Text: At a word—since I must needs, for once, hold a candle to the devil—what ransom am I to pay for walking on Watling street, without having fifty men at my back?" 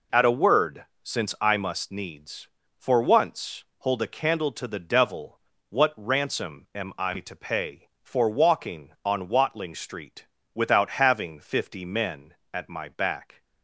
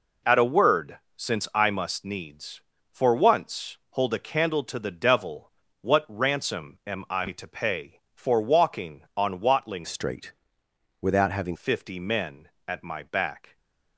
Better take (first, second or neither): first